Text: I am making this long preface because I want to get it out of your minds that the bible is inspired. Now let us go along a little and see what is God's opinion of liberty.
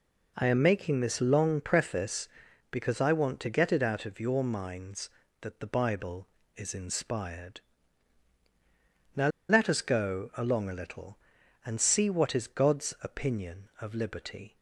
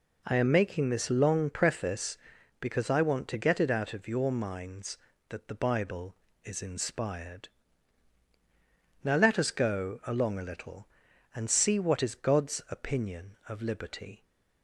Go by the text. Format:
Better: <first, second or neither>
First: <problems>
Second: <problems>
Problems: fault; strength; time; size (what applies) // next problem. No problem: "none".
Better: second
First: pauses between "Now" and "let"; slight; at 9.2 s; 0.21 s long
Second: none